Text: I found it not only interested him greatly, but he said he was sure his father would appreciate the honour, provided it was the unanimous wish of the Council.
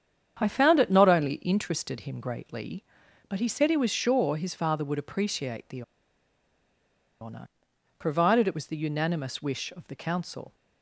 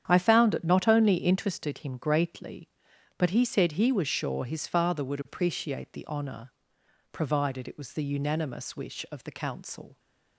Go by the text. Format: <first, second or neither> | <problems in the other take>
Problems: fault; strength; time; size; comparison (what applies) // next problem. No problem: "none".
second | starts louder than the rest; strong; until 1.4 s; 8.5 dB; strong in the second // pauses between "the" and "honour"; strong; at 5.8 s; 1.3 s long